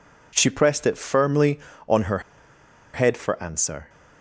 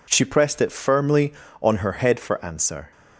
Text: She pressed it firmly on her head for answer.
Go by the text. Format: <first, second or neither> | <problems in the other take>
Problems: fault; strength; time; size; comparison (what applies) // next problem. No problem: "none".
second | pauses between "her" and "head"; noticeable; at 2.1 s; 0.74 s long